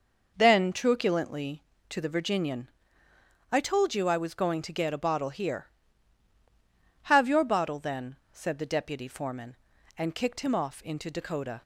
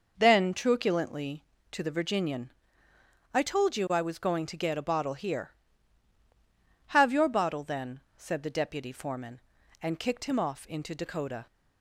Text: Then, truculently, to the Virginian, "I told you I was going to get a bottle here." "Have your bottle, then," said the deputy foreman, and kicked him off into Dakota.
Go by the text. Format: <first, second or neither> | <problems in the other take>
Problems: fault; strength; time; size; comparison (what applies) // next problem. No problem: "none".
neither | none